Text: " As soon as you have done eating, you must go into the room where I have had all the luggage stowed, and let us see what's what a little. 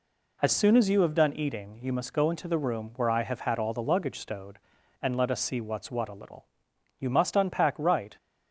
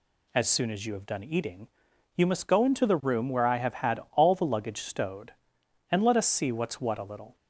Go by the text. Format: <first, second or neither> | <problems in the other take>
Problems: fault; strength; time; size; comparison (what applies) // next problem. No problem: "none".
second | goes on to say "You must unpack right"; noticeable; from 7.0 s on; 1.1 s long